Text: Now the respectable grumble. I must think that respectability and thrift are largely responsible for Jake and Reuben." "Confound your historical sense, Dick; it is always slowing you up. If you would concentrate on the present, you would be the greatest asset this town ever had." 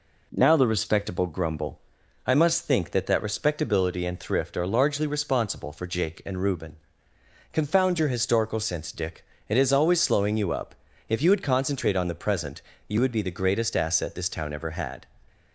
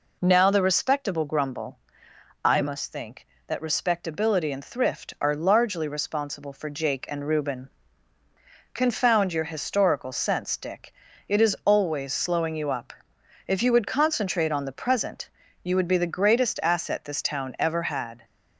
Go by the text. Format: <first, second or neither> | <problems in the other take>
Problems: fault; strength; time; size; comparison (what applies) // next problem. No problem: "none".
second | says "that" twice; at 3.0 s